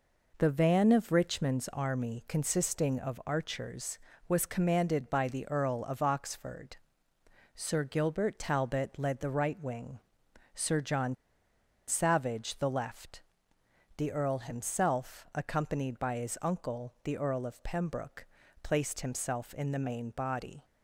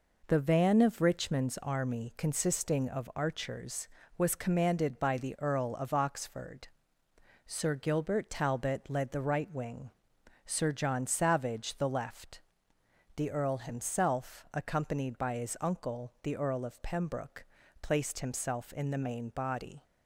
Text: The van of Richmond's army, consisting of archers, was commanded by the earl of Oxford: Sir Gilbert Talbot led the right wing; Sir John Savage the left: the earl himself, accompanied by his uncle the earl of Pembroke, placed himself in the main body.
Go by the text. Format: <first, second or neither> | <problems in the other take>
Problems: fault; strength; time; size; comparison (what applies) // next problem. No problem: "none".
second | pauses between "John" and "Savage"; noticeable; at 11.1 s; 0.73 s long